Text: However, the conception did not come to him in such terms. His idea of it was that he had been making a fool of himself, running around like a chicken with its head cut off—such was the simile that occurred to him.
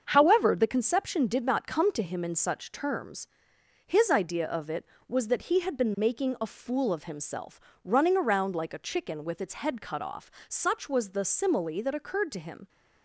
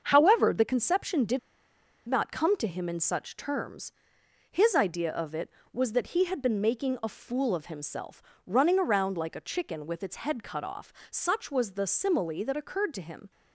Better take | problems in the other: first | starts louder than the rest; until 1.0 s; 6.5 dB; also in the first // pauses between "did" and "not"; noticeable; at 1.3 s; 0.68 s long

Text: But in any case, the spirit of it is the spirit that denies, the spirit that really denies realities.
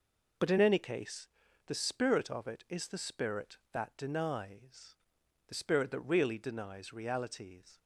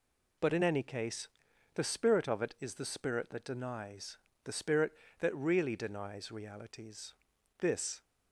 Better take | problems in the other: first | goes on to say "This"; slight; from 7.5 s on; 0.44 s long

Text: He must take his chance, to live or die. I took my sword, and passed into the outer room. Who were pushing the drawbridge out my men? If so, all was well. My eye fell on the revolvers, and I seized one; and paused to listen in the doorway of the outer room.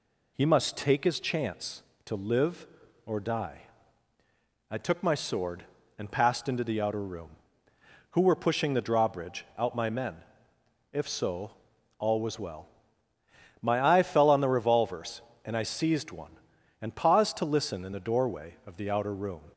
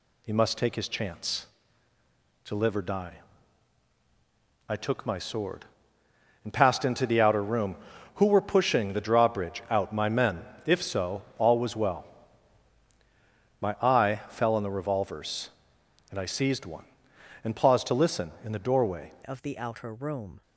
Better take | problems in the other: first | changes voice at "of"; from 19.2 s on; 1.2 s long

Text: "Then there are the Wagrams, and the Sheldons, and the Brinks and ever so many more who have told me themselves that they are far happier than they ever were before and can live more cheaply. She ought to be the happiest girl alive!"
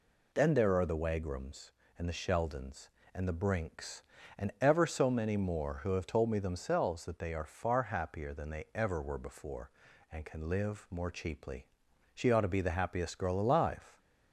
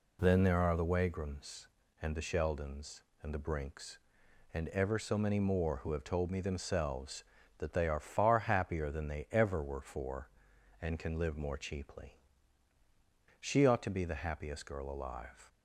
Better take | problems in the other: first | says "for" for "before"; at 9.8 s

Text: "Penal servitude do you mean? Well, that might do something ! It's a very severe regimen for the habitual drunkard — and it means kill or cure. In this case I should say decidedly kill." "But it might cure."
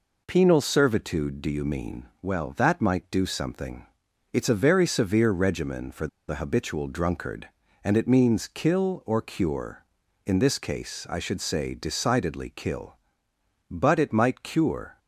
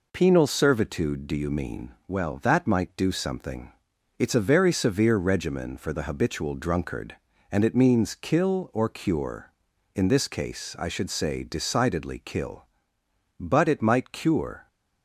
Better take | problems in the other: second | pauses between "for" and "the"; slight; at 6.0 s; 0.20 s long

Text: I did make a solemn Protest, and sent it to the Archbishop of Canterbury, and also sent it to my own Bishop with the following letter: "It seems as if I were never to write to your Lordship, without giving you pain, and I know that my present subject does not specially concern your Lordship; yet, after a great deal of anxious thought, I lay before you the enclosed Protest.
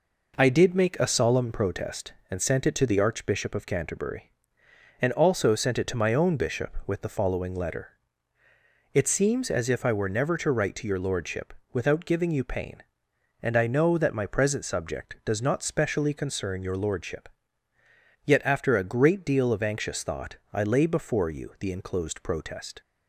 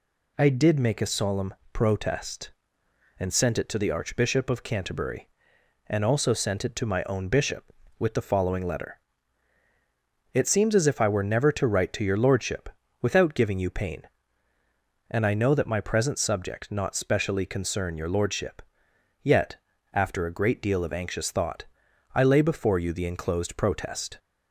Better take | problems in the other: first | pauses between "solemn" and "Protest"; slight; at 1.5 s; 0.18 s long // skips "does"; at 16.7 s

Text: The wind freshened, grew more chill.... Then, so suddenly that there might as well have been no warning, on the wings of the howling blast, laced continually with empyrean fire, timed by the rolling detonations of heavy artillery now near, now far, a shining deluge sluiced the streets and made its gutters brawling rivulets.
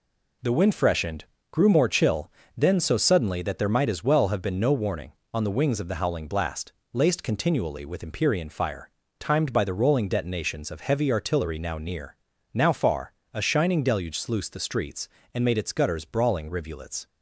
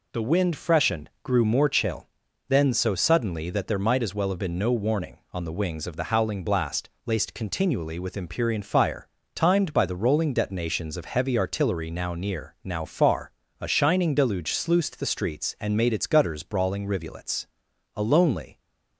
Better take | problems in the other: first | goes on to say "A lonely"; noticeable; from 17.9 s on; 0.64 s long

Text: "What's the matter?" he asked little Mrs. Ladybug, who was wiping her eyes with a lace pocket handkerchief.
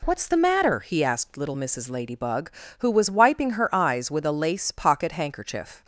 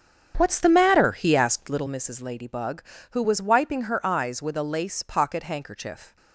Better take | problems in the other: first | starts louder than the rest; strong; until 2.0 s; 8 dB

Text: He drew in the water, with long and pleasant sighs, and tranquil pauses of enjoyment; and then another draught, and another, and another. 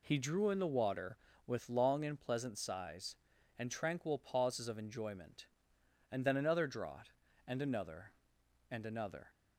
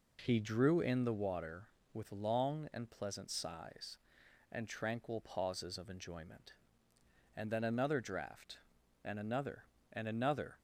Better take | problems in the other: neither | none

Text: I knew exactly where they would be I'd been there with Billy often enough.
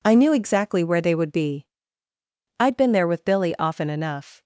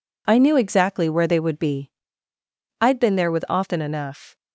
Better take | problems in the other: first | pauses between "be" and "I'd"; noticeable; at 1.9 s; 0.90 s long; noticeable in the first // skips "Billy"; at 3.4 s

